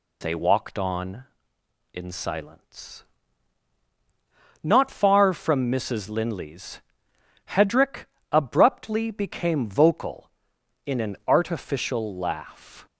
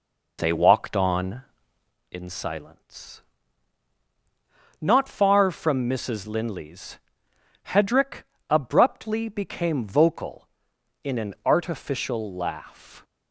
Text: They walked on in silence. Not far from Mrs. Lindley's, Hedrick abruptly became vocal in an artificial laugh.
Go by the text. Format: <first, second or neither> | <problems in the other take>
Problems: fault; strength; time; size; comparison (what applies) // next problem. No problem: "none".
first | starts louder than the rest; noticeable; until 2.0 s; 4.5 dB // pauses between "Hedrick" and "abruptly"; slight; at 8.2 s; 0.24 s long; slight in the first